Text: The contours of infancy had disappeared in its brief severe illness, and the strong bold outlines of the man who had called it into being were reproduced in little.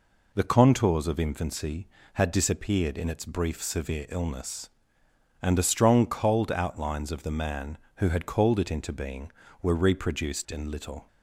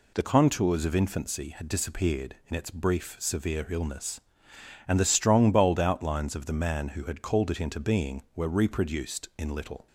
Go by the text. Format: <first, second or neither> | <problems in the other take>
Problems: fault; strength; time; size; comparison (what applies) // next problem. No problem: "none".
second | says "cold" for "bold"; at 6.0 s